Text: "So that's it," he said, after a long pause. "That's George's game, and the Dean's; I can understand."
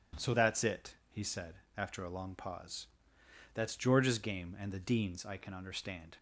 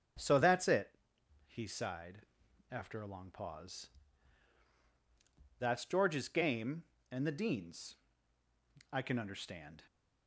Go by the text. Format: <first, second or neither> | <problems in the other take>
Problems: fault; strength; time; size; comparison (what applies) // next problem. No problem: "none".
first | starts louder than the rest; strong; until 1.7 s; 7 dB // says "sighed" for "said"; at 1.6 s